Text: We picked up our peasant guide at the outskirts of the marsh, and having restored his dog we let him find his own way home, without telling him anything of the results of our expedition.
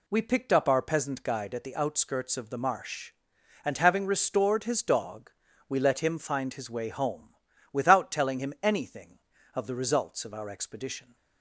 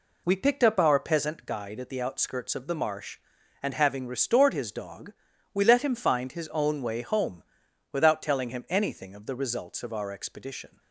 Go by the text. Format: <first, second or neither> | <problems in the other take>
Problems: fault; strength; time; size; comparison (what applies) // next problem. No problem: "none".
second | pauses between "dog" and "we"; at 5.3 s; 0.38 s long; also in the second // skips "own"; at 6.7 s